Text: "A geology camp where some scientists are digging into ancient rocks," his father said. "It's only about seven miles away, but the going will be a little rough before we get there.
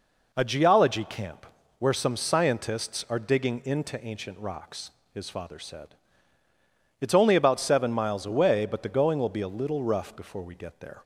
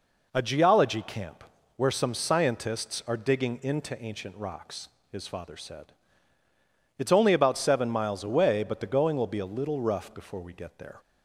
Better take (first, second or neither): neither